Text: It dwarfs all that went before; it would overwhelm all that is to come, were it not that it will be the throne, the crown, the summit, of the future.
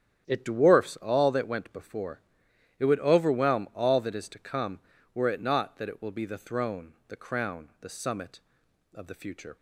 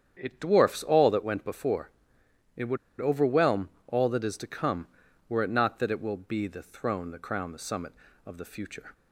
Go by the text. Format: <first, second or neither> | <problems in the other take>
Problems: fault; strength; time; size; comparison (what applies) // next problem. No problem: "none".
first | starts louder than the rest; strong; until 1.2 s; 8.5 dB; strong in the first // pauses between "would" and "overwhelm"; slight; at 2.7 s; 0.22 s long // pauses between "overwhelm" and "all"; slight; at 3.7 s; 0.18 s long